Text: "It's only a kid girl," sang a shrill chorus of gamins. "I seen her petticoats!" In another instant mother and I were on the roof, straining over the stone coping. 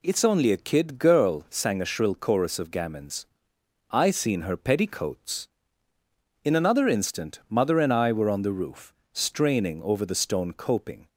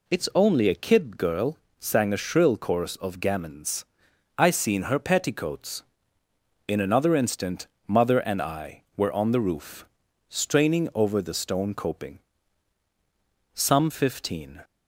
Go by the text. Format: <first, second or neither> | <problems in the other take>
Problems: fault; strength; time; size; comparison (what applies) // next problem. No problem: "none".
first | pauses between "instant" and "mother"; slight; at 7.6 s; 0.22 s long // goes on to say "Some fifteen"; noticeable; from 13.5 s on; 1.0 s long